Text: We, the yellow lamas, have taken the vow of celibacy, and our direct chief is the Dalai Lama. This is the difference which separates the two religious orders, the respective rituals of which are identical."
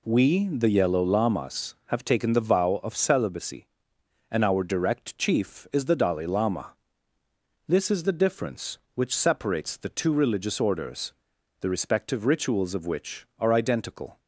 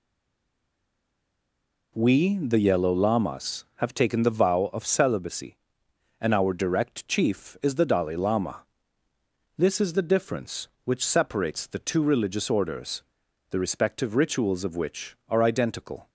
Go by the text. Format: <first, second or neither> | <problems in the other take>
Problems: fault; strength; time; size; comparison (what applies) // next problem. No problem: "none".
first | stays silent before the first word; noticeable; until 1.9 s; 1.9 s long